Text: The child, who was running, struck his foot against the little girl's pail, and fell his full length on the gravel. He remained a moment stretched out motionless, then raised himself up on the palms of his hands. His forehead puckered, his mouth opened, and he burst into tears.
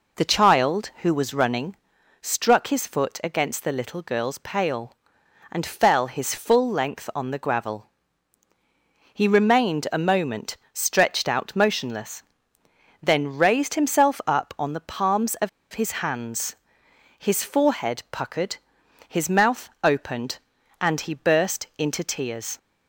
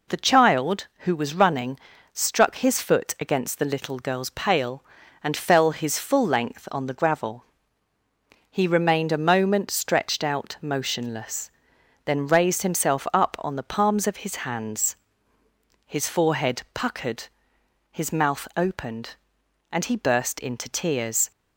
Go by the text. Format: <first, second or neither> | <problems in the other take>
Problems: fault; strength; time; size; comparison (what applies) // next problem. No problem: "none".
second | pauses between "moment" and "stretched"; slight; at 10.5 s; 0.16 s long // pauses between "of" and "his"; slight; at 15.4 s; 0.23 s long